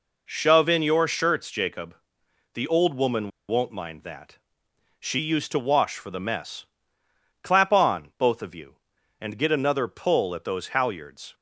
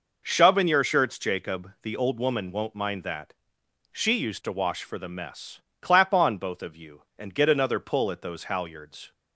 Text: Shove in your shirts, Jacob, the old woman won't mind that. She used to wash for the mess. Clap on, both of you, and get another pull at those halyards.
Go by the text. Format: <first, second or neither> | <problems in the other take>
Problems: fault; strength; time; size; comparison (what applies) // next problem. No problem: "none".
second | pauses between "woman" and "won't"; slight; at 3.3 s; 0.18 s long